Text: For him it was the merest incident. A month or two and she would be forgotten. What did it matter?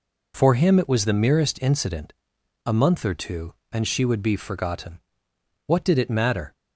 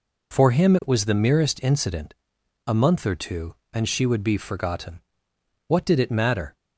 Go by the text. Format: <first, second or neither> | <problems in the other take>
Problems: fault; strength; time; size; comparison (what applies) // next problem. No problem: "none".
neither | none